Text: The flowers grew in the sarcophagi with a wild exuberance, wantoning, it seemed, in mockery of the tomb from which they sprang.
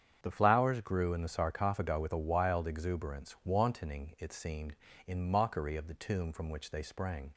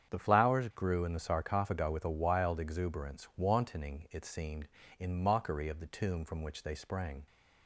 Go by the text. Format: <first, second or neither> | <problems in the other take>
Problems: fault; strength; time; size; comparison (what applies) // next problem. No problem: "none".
neither | starts louder than the rest; strong; the same in both